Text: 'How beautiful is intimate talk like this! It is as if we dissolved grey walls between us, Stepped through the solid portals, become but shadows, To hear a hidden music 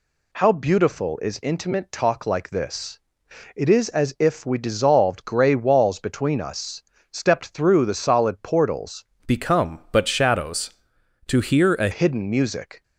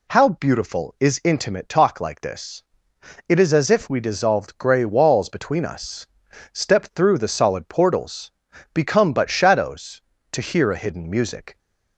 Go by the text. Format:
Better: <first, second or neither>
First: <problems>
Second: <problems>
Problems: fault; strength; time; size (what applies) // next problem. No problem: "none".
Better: second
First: changes voice from "become" to "a"; from 9.2 to 11.8 s; 2.6 s long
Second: none